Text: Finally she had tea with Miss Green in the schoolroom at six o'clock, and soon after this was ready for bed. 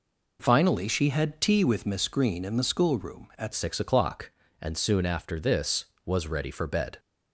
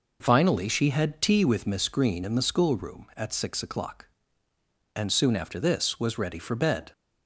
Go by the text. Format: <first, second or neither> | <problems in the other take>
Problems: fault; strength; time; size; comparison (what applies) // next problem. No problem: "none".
second | changes voice at "six"; from 3.5 s on; 3.4 s long